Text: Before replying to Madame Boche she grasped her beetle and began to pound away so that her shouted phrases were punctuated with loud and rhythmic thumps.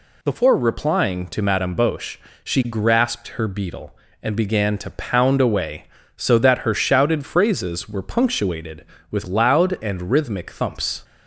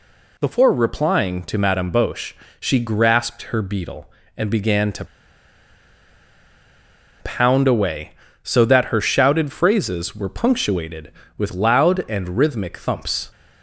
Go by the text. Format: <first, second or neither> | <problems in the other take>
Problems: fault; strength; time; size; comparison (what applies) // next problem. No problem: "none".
first | pauses between "Boche" and "she"; slight; at 2.3 s; 0.24 s long; slight in the first // pauses between "to" and "pound"; strong; at 5.0 s; 2.1 s long